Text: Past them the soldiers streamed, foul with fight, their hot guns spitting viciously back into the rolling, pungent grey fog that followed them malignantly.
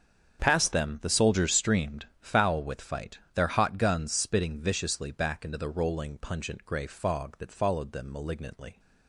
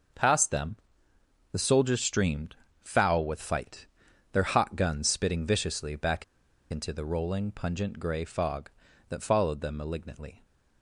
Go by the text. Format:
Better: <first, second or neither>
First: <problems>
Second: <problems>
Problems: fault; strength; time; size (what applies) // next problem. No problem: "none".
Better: first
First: starts louder than the rest; strong; until 1.4 s; 7.5 dB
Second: starts louder than the rest; until 1.9 s; 6.5 dB // pauses between "them" and "the"; noticeable; at 0.7 s; 0.76 s long // pauses between "back" and "into"; noticeable; at 6.2 s; 0.46 s long